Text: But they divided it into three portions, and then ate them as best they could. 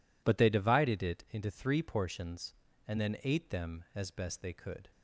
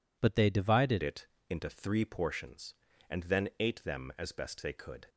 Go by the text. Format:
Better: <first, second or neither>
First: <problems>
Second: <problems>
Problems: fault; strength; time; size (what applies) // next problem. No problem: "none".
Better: first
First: none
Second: changes voice at "it"; from 1.0 s on; 4.0 s long // pauses between "it" and "into"; slight; at 1.2 s; 0.22 s long